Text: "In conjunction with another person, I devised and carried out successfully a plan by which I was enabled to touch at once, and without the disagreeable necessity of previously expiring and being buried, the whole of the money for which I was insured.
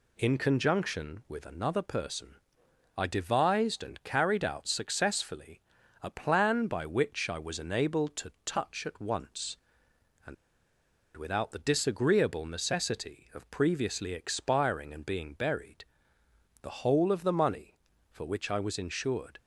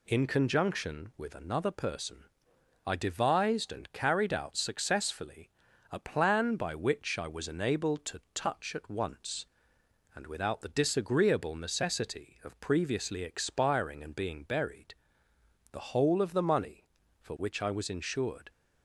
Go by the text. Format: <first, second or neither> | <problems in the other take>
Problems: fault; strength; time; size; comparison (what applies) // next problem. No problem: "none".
second | pauses between "successfully" and "a"; at 5.5 s; 0.42 s long; also in the second // pauses between "and" and "without"; noticeable; at 10.3 s; 0.81 s long